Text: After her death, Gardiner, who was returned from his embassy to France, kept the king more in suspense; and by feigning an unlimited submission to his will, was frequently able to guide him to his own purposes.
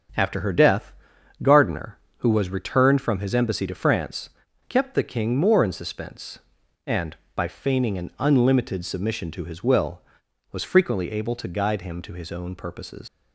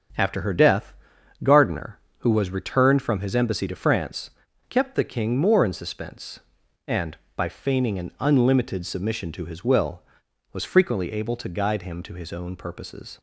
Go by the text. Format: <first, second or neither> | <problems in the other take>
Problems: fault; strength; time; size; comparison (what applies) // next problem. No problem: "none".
second | starts louder than the rest; strong; until 1.6 s; 7.5 dB; strong in the second // leaves "purposes" unfinished; at 13.0 s; 105 ms